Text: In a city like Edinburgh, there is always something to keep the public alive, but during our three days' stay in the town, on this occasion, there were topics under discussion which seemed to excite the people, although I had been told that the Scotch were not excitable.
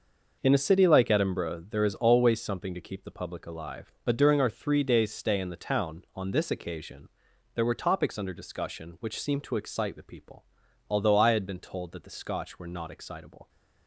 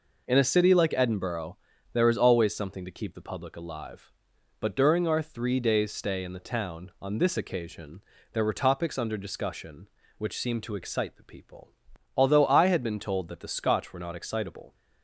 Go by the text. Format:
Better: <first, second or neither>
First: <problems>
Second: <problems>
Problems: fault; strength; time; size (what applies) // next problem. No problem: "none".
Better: neither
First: none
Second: none